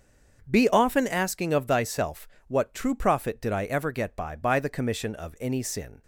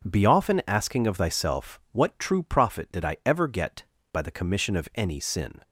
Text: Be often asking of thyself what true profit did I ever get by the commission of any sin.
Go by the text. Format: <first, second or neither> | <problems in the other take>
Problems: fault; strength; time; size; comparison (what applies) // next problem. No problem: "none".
second | starts louder than the rest; until 1.4 s; 6.5 dB // pauses between "thyself" and "what"; slight; at 2.2 s; 0.20 s long // says "by" twice; at 4.3 s